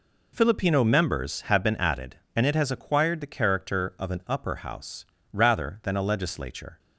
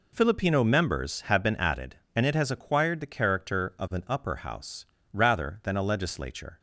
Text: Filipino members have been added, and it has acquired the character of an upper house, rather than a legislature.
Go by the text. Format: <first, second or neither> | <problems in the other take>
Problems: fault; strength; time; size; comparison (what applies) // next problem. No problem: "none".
neither | none